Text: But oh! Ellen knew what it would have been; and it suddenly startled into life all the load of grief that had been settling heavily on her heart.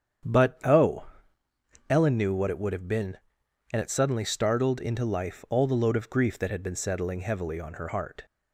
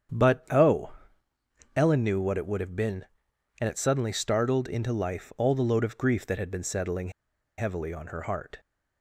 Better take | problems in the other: first | starts louder than the rest; strong; until 2.0 s; 8.5 dB; strong in the first // pauses between "settling" and "heavily"; noticeable; at 7.1 s; 0.47 s long

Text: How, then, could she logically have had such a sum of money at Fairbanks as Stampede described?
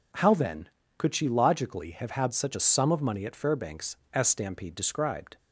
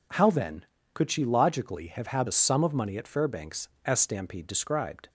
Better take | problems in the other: first | skips "such"; at 2.2 s

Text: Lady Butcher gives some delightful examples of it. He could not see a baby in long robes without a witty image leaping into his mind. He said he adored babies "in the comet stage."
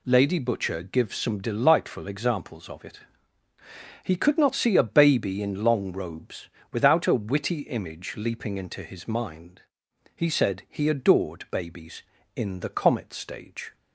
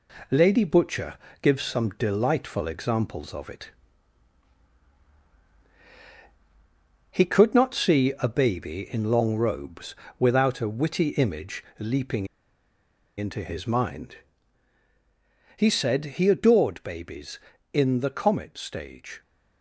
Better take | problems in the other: first | pauses between "Butcher" and "gives"; slight; at 1.1 s; 0.26 s long // pauses between "robes" and "without"; slight; at 9.9 s; 0.24 s long; slight in the first // pauses between "image" and "leaping"; slight; at 11.6 s; 0.16 s long // pauses between "leaping" and "into"; noticeable; at 12.2 s; 0.90 s long

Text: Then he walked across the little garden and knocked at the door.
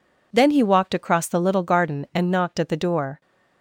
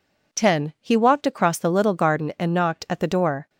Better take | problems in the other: first | says "Ten" for "Then"; at 0.3 s

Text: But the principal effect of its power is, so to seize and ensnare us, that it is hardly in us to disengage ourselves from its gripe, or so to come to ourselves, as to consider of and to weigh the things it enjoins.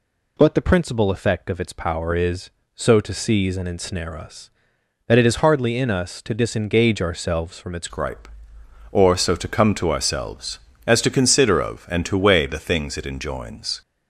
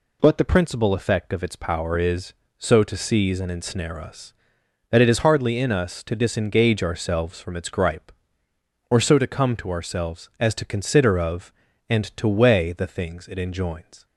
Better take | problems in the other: second | changes voice at "gripe"; from 7.8 s on; 6.0 s long

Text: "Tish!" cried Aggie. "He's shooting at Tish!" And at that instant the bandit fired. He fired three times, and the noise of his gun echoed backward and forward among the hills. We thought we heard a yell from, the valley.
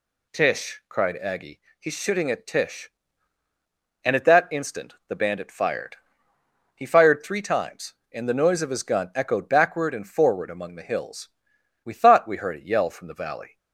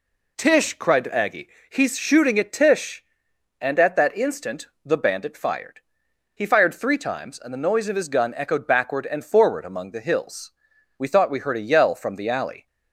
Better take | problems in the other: first | pauses between "instant" and "the"; slight; at 4.6 s; 0.18 s long // says "alley" for "valley"; at 12.2 s

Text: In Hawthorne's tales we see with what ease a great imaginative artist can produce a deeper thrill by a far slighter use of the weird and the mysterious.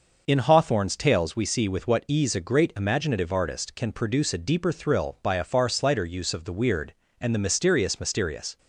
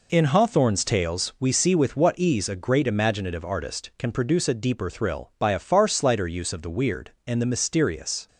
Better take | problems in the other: second | says "mysterious" twice; at 7.9 s

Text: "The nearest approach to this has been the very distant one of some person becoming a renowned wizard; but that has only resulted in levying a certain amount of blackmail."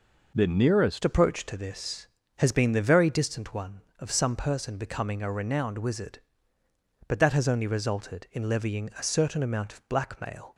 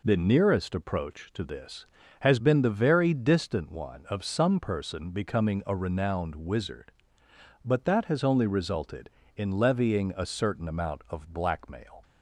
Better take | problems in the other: second | changes voice at "approach"; from 1.0 s on; 9.5 s long

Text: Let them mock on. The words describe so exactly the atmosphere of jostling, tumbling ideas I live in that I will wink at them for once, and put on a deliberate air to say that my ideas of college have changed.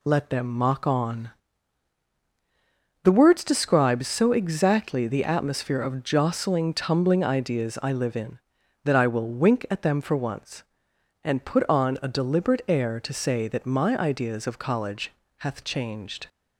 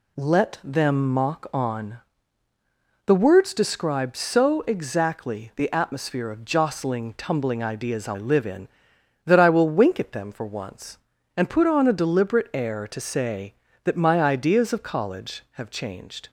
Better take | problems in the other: second | says "hath" for "have"; at 15.3 s

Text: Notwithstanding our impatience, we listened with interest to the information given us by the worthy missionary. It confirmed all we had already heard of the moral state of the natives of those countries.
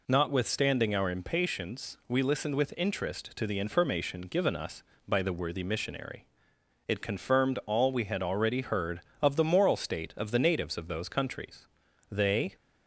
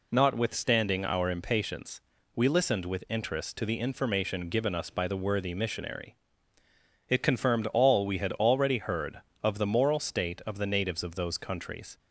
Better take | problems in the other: second | goes on to say "They"; slight; from 12.1 s on; 0.44 s long

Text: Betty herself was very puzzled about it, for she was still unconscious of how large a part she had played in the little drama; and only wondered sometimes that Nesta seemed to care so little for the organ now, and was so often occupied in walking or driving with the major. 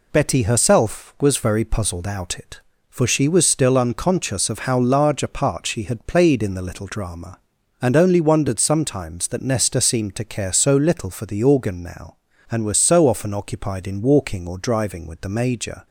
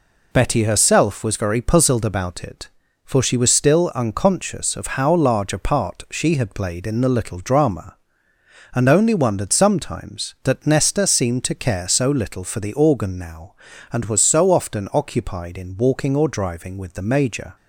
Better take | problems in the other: second | says "out" for "about"; at 2.0 s

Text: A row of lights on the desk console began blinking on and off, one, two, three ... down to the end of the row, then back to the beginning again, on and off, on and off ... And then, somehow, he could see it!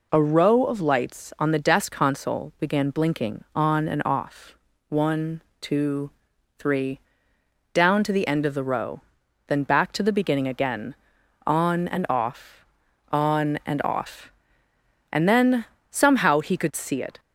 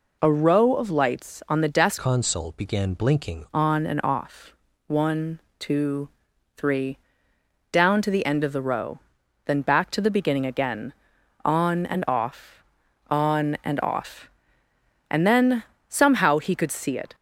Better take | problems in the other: first | changes voice from "console" to "blinking"; from 1.9 to 3.4 s; 1.5 s long

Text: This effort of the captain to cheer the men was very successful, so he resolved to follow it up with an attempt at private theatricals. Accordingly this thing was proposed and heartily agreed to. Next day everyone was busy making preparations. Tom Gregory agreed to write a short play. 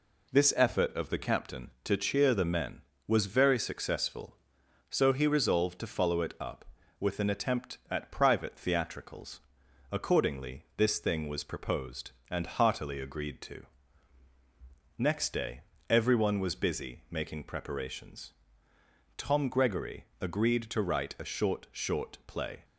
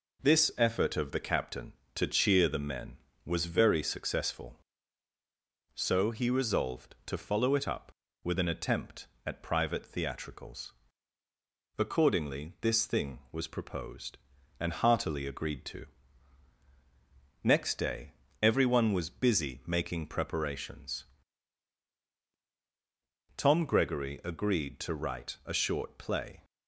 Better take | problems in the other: second | pauses between "day" and "everyone"; slight; at 15.6 s; 0.26 s long; slight in the second // pauses between "Gregory" and "agreed"; slight; at 20.0 s; 0.16 s long // says "short" twice; at 21.7 s

